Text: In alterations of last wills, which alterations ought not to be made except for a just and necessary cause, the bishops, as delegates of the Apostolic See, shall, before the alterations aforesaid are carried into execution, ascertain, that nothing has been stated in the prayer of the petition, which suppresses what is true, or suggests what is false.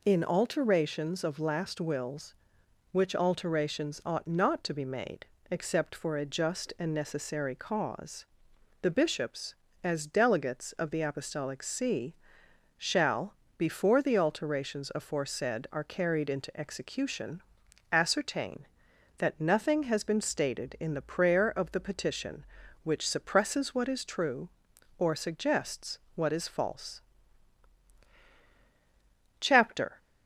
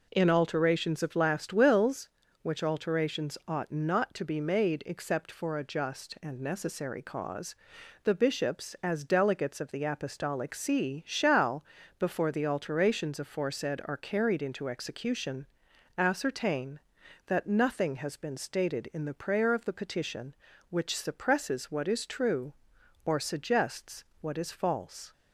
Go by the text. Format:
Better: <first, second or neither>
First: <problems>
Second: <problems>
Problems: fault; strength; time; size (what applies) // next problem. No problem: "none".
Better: second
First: pauses between "made" and "except"; slight; at 5.2 s; 0.22 s long // pauses between "suggests" and "what"; slight; at 25.9 s; 0.16 s long // goes on to say "CHAPTER"; from 29.3 s on; 0.58 s long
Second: pauses between "suggests" and "what"; slight; at 24.0 s; 0.18 s long